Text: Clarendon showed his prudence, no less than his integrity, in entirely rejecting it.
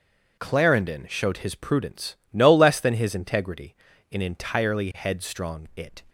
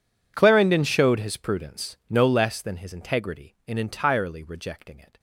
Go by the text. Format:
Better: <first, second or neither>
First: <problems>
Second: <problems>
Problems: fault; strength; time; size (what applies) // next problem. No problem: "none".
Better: second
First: says "headstrong" for "rejecting"; at 4.9 s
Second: none